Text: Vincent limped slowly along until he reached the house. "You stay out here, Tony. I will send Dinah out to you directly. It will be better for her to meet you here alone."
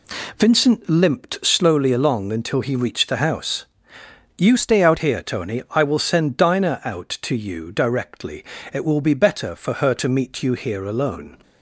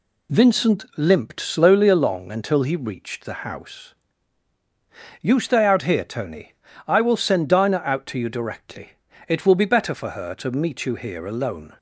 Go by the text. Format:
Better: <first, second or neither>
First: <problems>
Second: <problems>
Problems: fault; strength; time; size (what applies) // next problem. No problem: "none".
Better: second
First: changes voice from "stay" to "out"; from 4.5 to 4.9 s; 0.4 s long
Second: none